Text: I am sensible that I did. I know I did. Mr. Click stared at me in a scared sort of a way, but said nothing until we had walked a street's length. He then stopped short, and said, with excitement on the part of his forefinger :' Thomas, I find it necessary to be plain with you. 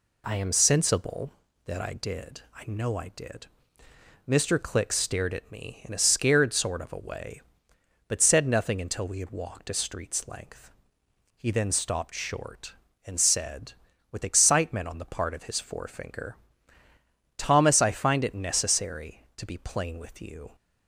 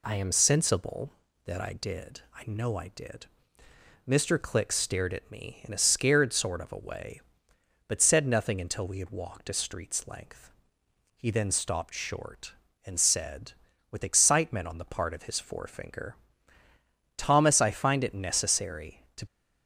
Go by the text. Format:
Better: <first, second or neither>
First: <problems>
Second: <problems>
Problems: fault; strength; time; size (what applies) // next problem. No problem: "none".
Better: first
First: none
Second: stops before "be plain with you"; at 19.2 s